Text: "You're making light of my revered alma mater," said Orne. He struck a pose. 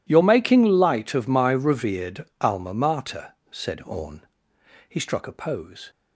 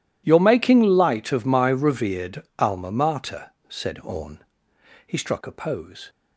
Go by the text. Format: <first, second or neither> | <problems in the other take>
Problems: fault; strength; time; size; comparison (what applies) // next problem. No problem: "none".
neither | none